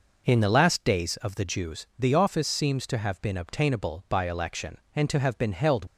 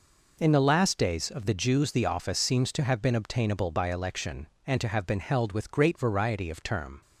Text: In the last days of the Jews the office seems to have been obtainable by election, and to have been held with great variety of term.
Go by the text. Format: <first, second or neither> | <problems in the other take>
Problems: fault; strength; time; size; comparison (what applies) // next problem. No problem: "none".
second | stops before "with great variety of term"; at 5.8 s